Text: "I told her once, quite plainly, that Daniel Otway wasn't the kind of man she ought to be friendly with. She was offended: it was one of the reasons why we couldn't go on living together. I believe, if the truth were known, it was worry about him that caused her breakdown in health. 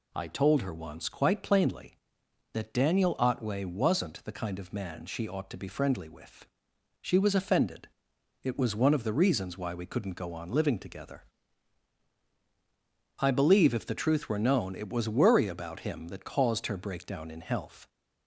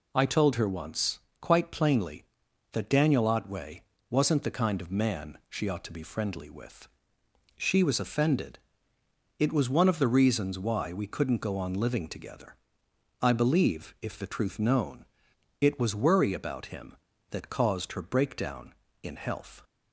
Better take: first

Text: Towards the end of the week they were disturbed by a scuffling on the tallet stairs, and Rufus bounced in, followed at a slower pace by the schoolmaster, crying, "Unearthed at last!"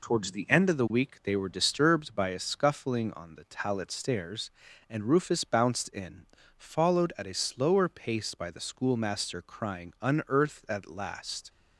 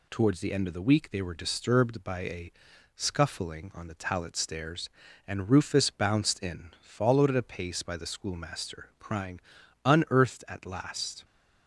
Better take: first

